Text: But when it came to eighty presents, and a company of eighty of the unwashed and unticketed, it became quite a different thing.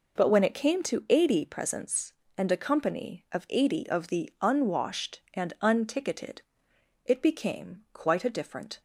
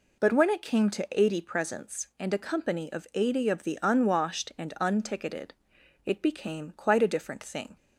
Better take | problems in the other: second | stops before "thing"; at 8.7 s

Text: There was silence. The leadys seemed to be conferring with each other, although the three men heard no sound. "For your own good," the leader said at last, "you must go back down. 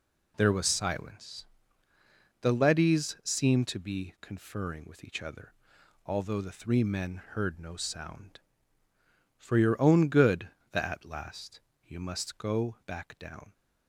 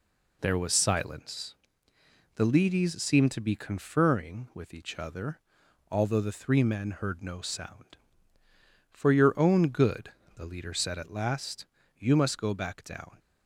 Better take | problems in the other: second | skips "leader said"; at 10.8 s

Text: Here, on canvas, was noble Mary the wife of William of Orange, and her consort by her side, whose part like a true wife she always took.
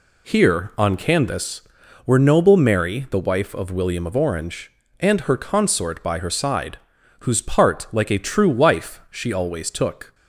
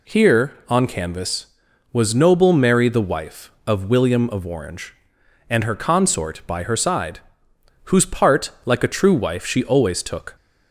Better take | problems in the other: second | says "were" for "was"; at 2.0 s

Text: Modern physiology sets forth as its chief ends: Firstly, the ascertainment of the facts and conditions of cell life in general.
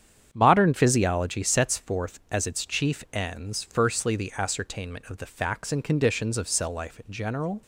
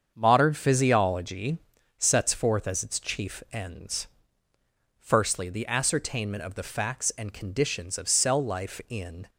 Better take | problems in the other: first | starts louder than the rest; strong; until 1.1 s; 7 dB; strong in the first // pauses between "physiology" and "sets"; at 1.5 s; 0.38 s long // stops before "general"; at 9.2 s

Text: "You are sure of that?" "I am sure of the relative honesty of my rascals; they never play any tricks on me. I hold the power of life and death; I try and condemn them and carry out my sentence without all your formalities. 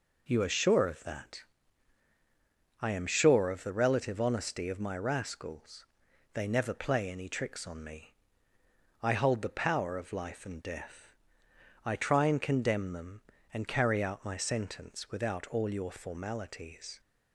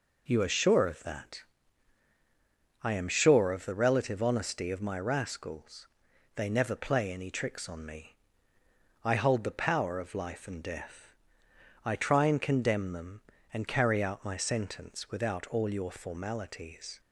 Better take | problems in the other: neither | none

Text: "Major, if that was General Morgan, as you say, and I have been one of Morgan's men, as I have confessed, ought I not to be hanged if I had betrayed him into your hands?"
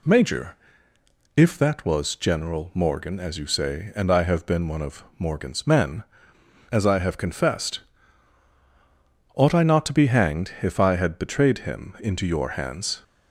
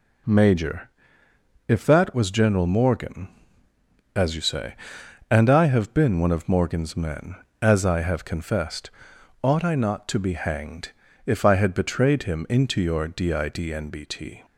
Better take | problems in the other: first | pauses between "hanged" and "if"; slight; at 10.9 s; 0.34 s long // says "didnbt" for "hands"; at 13.0 s

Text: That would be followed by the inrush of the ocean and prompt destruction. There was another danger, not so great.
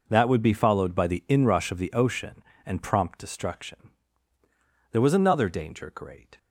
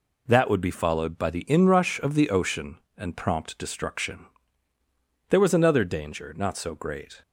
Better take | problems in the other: second | skips "not so"; at 5.9 s

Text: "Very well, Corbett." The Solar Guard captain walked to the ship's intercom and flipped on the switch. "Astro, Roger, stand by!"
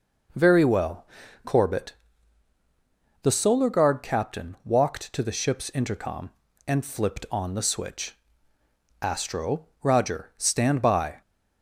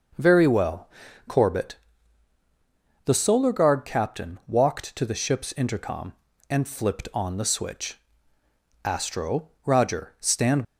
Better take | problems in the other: first | stops before "by"; at 10.6 s

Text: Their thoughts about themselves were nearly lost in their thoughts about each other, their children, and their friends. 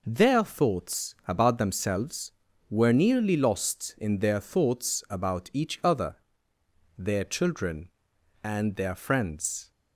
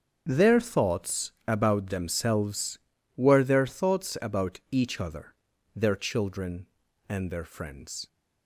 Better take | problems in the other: first | starts louder than the rest; until 1.2 s; 7 dB // pauses between "thoughts" and "about"; slight; at 1.3 s; 0.16 s long // skips "nearly lost in"; at 3.4 s

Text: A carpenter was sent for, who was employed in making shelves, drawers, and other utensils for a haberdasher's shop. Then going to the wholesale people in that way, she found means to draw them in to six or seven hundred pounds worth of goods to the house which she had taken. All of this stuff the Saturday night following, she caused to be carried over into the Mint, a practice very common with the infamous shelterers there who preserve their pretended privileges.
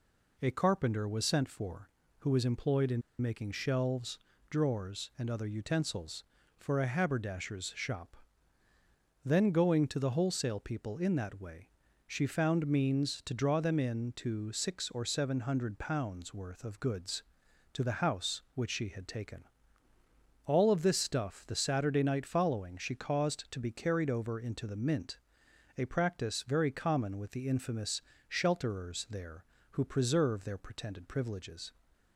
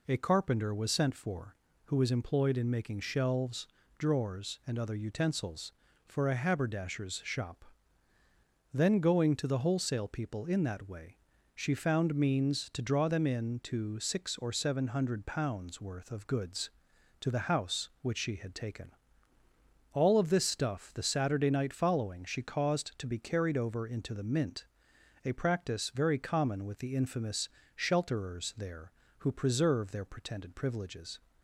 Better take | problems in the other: second | pauses between "in" and "making"; slight; at 3.0 s; 0.20 s long // pauses between "infamous" and "shelterers"; slight; at 27.9 s; 0.30 s long; slight in the second

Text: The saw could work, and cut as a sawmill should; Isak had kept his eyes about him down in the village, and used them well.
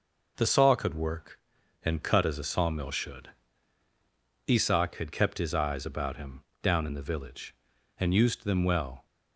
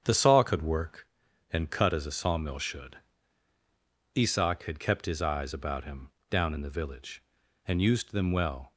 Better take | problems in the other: first | starts louder than the rest; strong; until 1.1 s; 8 dB // pauses between "him" and "down"; slight; at 6.1 s; 0.18 s long; slight in the first

